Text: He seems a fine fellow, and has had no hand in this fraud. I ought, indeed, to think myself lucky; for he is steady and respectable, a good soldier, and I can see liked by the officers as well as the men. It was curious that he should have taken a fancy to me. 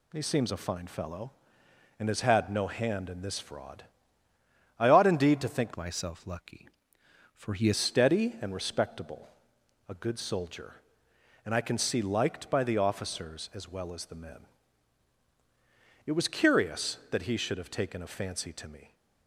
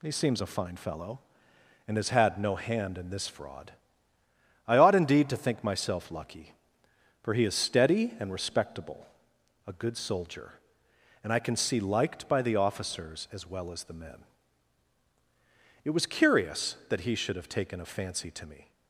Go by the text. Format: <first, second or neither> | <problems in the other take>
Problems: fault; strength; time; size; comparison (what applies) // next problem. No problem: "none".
second | changes voice from "myself" to "is"; from 5.7 to 7.7 s; 2.0 s long